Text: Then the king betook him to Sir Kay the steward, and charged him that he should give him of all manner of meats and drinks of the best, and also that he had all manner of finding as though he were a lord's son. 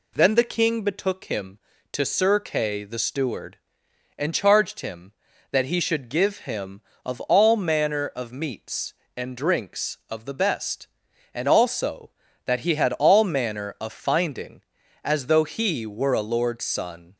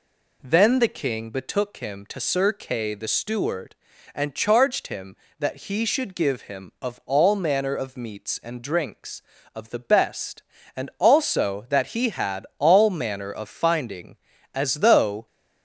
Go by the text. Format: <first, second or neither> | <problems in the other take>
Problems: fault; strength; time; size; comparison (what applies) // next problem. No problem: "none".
first | stops before "he were a lord's son"; at 15.2 s